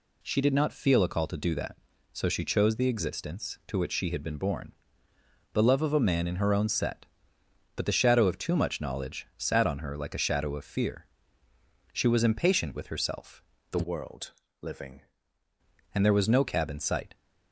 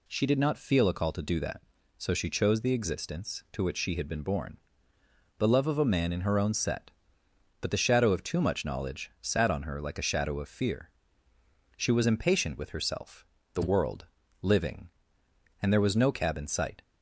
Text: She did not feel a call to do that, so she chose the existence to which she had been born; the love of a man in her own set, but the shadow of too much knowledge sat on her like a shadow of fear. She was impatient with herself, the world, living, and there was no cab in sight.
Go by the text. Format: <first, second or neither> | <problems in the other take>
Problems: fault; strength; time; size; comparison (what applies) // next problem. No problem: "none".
second | changes voice from "world" to "living"; from 13.8 to 15.0 s; 1.2 s long